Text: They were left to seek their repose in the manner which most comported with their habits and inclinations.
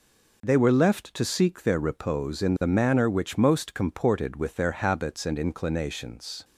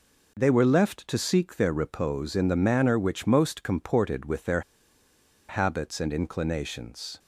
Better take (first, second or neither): first